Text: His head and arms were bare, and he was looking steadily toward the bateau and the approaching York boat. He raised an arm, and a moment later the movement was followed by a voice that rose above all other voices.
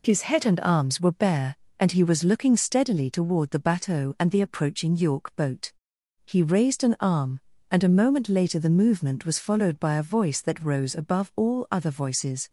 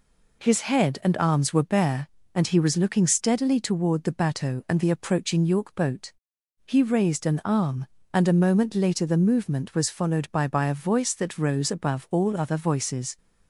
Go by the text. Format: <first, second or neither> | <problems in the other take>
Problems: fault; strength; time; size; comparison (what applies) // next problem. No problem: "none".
first | says "by" twice; at 10.4 s